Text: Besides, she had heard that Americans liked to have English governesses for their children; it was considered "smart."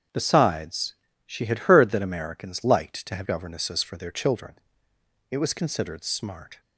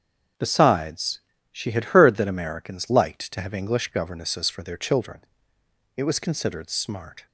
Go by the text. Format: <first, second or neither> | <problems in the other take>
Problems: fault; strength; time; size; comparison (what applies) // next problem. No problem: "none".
second | starts louder than the rest; strong; until 1.4 s; 8 dB; strong in the second // skips "English"; at 3.2 s